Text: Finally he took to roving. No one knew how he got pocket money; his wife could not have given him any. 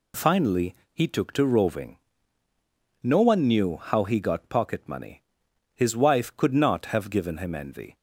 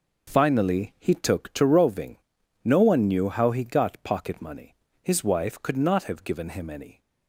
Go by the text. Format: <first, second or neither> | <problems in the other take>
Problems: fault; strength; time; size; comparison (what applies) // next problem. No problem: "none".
second | pauses between "Finally" and "he"; slight; at 0.7 s; 0.20 s long // says "envy" for "any"; at 7.5 s